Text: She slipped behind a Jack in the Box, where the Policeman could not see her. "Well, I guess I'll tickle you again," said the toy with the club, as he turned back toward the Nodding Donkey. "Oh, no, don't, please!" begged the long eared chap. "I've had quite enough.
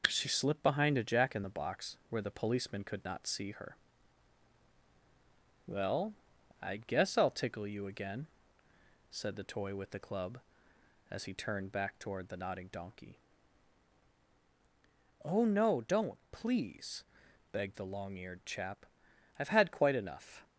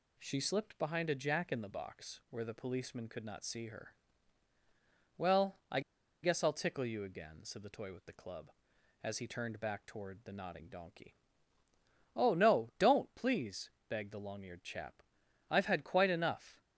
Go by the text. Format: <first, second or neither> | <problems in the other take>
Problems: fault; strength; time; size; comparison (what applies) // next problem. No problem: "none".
first | pauses between "I" and "guess"; at 5.7 s; 0.44 s long